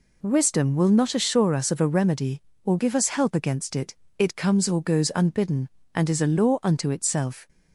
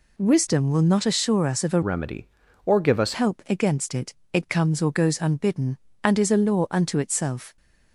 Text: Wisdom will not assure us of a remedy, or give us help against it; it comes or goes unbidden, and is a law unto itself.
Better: first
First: none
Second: changes voice from "remedy" to "us"; from 1.8 to 3.1 s; 1.3 s long

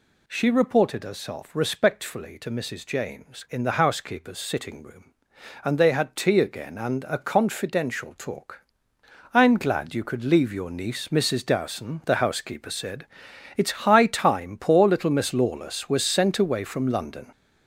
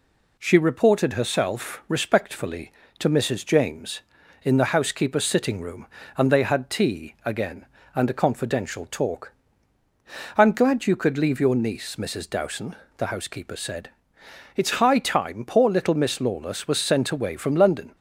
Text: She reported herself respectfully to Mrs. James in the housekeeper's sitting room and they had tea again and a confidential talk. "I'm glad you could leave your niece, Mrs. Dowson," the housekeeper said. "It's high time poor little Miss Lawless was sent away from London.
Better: second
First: gets louder; throughout; 6.5 dB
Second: none

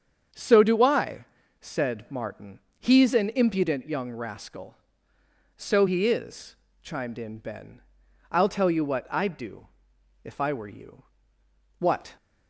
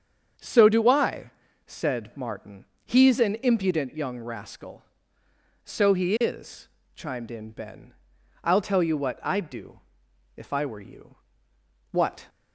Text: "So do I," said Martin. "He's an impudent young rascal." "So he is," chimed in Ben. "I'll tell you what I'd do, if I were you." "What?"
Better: neither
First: starts louder than the rest; strong; until 1.6 s; 7 dB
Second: starts louder than the rest; strong; until 1.7 s; 7.5 dB

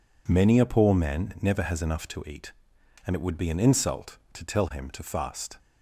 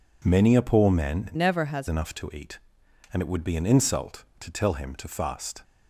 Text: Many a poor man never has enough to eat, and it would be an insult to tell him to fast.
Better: first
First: none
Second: changes voice from "never" to "has"; from 1.3 to 1.8 s; 0.5 s long

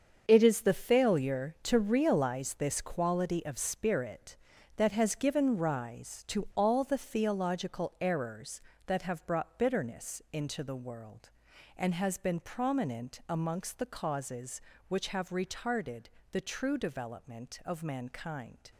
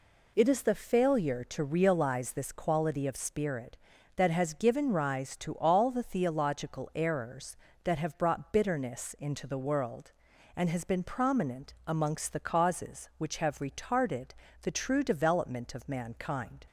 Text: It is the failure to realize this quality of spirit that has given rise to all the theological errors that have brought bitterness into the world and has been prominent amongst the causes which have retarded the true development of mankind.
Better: second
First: gets quieter; strong; throughout; 11 dB // pauses between "retarded" and "the"; slight; at 16.0 s; 0.24 s long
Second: pauses between "retarded" and "the"; slight; at 14.2 s; 0.32 s long

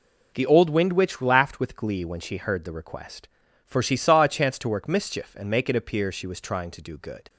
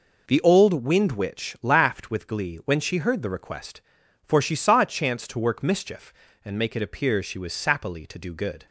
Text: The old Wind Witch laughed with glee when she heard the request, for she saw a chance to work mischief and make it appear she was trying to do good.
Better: first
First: none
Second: says "sappily" for "trying"; at 7.5 s

